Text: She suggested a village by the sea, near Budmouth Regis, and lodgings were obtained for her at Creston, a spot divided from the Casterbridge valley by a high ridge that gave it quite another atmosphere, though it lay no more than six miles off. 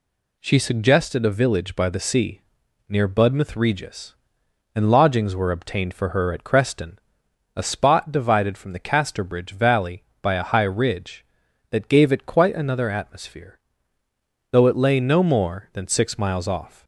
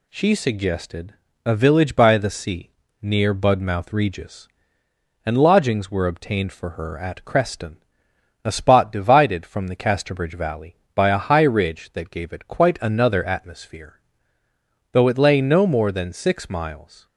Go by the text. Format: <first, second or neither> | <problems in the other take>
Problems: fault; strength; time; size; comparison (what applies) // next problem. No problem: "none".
first | pauses between "suggested" and "a"; slight; at 1.1 s; 0.32 s long // stops before "off"; at 17.0 s